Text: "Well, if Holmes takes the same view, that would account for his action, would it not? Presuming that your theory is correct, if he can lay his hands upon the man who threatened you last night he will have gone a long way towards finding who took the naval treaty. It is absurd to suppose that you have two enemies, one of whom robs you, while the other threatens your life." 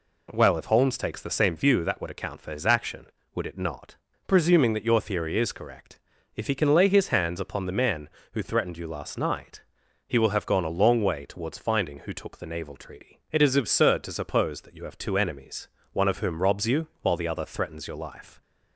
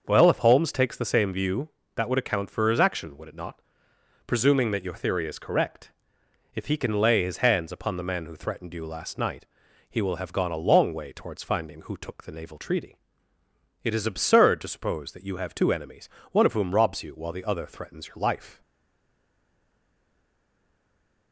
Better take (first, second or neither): first